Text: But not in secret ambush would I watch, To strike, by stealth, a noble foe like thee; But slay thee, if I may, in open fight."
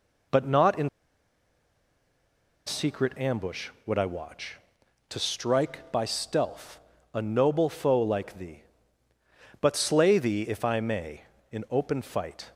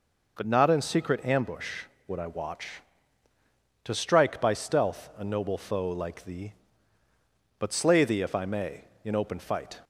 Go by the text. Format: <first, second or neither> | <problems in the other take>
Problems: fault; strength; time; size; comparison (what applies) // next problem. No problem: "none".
second | pauses between "in" and "secret"; strong; at 0.8 s; 1.7 s long